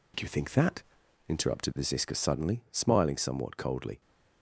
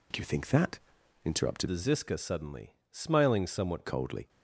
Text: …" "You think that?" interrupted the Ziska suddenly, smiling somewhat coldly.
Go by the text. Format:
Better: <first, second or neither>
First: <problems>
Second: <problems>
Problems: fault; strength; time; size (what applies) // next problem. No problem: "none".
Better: first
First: none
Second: changes voice from "the" to "somewhat"; from 1.6 to 3.8 s; 2.2 s long